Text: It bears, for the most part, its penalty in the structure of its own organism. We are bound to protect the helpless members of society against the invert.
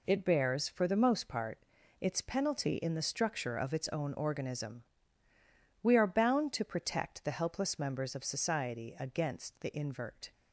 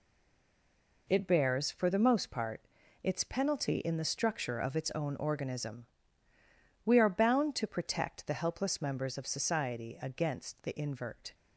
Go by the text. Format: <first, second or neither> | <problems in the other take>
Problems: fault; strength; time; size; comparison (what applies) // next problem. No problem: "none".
first | stays silent before the first word; until 1.0 s; 1.0 s long